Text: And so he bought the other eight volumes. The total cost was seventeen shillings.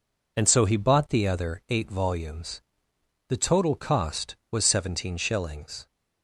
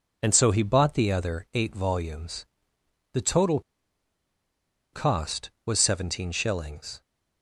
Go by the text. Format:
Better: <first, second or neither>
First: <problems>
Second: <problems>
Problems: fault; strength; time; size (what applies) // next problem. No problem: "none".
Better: first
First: none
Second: pauses between "total" and "cost"; strong; at 3.6 s; 1.3 s long